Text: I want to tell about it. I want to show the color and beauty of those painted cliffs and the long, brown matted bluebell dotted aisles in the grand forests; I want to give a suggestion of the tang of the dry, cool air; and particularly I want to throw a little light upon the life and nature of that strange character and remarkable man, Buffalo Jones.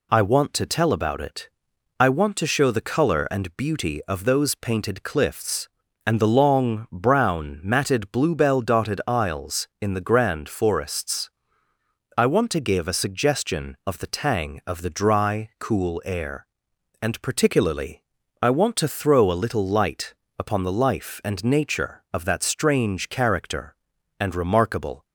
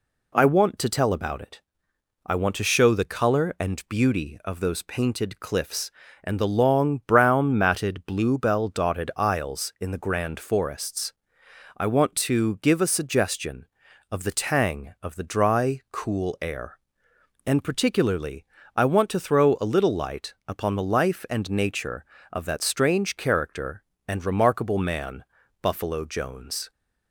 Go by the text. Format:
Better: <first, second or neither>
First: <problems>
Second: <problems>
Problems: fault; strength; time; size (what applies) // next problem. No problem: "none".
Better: second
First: pauses between "particularly" and "I"; at 18.0 s; 0.38 s long // pauses between "light" and "upon"; slight; at 20.1 s; 0.24 s long // stops before "man Buffalo Jones"; at 25.0 s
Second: pauses between "particularly" and "I"; slight; at 18.4 s; 0.32 s long